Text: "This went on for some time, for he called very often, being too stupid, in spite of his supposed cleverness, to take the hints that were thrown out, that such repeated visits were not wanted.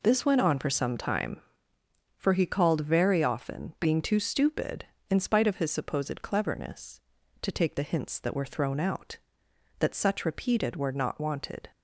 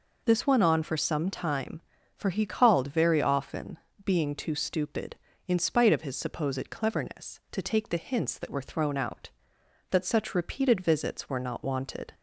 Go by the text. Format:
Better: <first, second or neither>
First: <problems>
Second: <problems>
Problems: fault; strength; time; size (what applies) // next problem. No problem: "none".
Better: second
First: skips "visits"; at 10.7 s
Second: none